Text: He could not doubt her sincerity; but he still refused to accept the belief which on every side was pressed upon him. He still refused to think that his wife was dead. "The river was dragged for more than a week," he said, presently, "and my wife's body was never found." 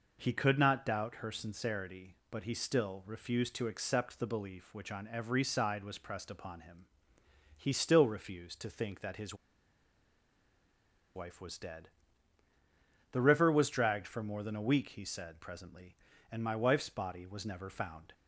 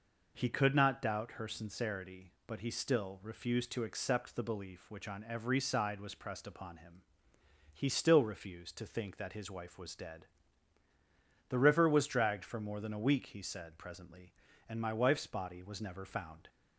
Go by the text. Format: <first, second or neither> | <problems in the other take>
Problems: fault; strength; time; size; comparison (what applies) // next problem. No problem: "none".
second | pauses between "his" and "wife"; strong; at 9.3 s; 1.8 s long